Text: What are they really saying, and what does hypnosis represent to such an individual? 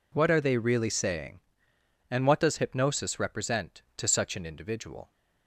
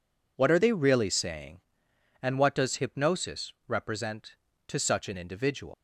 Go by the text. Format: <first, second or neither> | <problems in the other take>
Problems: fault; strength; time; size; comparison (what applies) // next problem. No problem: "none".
first | leaves "individual" unfinished; at 5.7 s; 145 ms